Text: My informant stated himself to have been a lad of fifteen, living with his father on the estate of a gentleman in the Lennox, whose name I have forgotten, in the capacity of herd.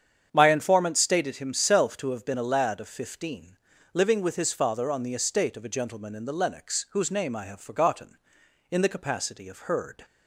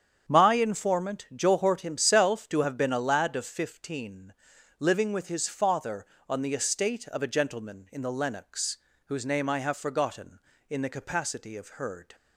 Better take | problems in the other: first | starts louder than the rest; strong; until 1.3 s; 8.5 dB; strong in the first // says "johort" for "stated"; at 1.3 s

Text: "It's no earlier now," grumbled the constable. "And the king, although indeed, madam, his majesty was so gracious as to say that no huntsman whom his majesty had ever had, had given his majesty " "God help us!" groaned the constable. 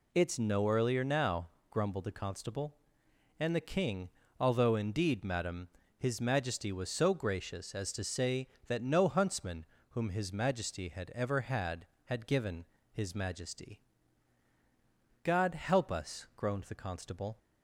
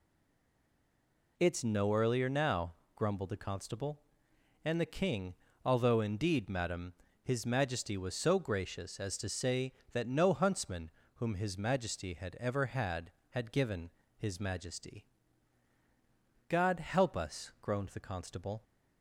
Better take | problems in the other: first | stays silent before the first word; noticeable; until 1.3 s; 1.3 s long // pauses between "huntsman" and "whom"; slight; at 10.9 s; 0.24 s long; slight in the first // pauses between "given" and "his"; slight; at 13.8 s; 0.28 s long; slight in the first

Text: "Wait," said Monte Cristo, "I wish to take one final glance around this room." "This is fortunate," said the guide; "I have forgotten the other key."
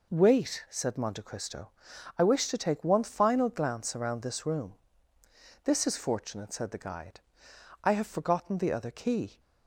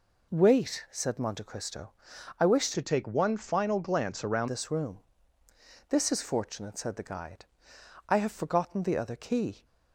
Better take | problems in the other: first | changes voice from "to" to "around"; from 2.7 to 4.4 s; 1.7 s long

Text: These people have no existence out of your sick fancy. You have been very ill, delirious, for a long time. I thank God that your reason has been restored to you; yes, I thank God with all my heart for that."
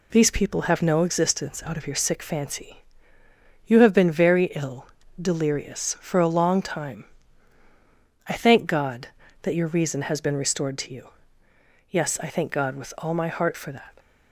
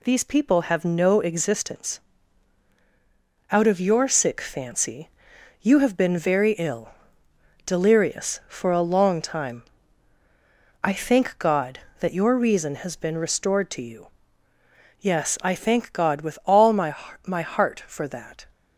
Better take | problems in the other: first | pauses between "existence" and "out"; strong; at 1.9 s; 1.5 s long // says "my" twice; at 17.2 s

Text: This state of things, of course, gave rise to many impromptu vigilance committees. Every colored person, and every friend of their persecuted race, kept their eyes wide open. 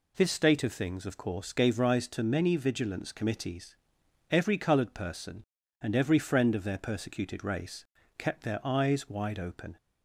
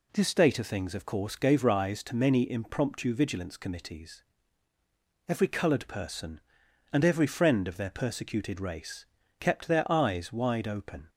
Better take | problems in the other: second | skips "impromptu"; at 2.5 s

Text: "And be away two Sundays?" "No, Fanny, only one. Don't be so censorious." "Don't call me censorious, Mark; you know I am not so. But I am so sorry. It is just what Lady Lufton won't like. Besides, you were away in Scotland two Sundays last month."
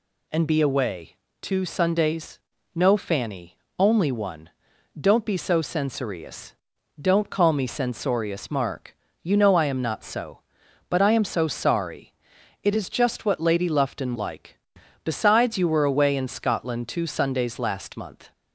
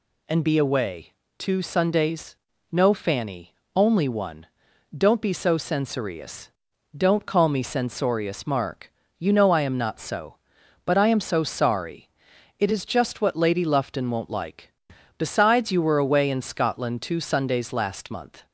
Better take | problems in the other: second | pauses between "away" and "two"; slight; at 1.1 s; 0.24 s long; slight in the second // skips "won't"; at 14.1 s

